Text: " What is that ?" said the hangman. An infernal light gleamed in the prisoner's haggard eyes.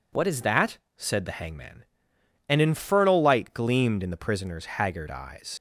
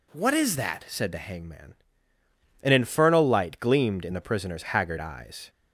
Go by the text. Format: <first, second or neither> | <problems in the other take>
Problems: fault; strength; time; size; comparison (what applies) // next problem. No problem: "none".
second | leaves "eyes" unfinished; at 5.5 s; 50 ms